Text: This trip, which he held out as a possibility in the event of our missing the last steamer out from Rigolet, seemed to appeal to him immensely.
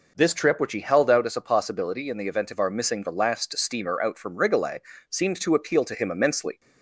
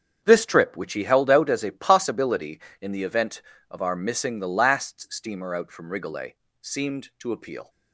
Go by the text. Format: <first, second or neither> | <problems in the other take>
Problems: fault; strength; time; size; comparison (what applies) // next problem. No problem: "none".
first | starts louder than the rest; strong; until 1.2 s; 7.5 dB // stops before "to him immensely"; at 7.6 s